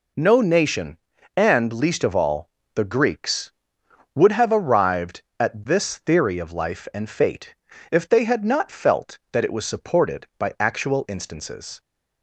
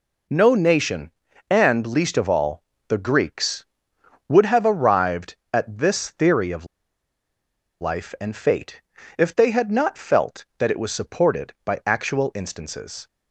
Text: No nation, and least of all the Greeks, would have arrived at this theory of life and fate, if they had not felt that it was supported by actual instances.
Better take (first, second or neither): first